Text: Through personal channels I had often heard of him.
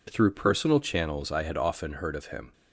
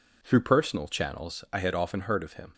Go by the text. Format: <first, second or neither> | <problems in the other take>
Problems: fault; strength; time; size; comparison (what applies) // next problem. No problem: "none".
neither | none